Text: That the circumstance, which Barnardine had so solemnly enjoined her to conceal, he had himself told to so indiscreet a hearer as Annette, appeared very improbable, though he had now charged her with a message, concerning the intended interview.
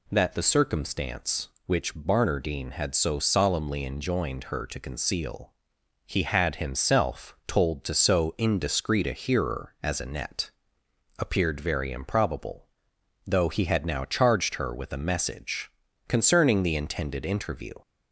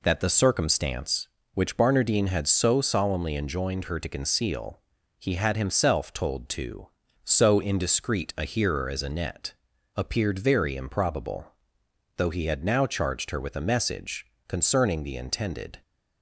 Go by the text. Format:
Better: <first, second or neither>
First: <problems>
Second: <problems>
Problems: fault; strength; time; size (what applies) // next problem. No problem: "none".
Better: first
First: none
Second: stops before "interview"; at 15.8 s